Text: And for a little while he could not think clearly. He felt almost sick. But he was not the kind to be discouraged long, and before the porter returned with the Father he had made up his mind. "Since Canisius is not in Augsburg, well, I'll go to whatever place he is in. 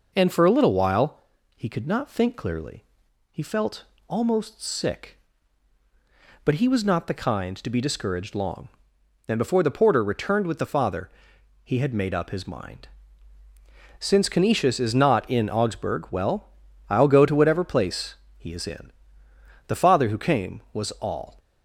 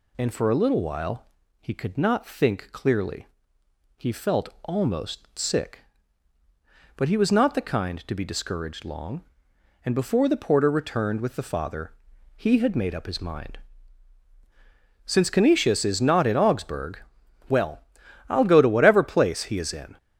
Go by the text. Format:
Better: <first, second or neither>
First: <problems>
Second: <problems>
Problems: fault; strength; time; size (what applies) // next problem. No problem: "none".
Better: second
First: pauses between "while" and "he"; at 1.1 s; 0.38 s long // pauses between "felt" and "almost"; slight; at 3.8 s; 0.24 s long // pauses between "Father" and "he"; noticeable; at 11.0 s; 0.54 s long // pauses between "place" and "he"; slight; at 18.1 s; 0.20 s long // goes on to say "The Father who came was all"; strong; from 19.6 s on; 1.7 s long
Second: pauses between "while" and "he"; slight; at 1.2 s; 0.36 s long // pauses between "felt" and "almost"; slight; at 4.4 s; 0.16 s long // pauses between "Father" and "he"; at 11.9 s; 0.44 s long